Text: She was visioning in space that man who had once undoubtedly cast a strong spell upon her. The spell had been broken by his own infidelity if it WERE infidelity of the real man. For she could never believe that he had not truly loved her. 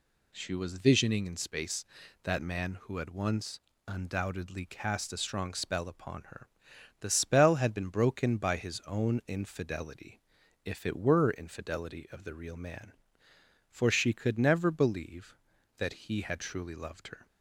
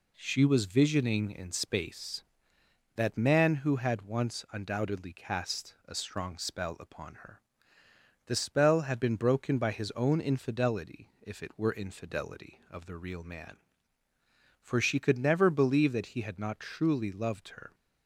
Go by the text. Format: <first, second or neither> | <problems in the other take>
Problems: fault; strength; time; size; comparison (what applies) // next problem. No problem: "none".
second | pauses between "once" and "undoubtedly"; slight; at 3.5 s; 0.26 s long // pauses between "infidelity" and "if"; at 10.1 s; 0.44 s long // skips "not"; at 16.3 s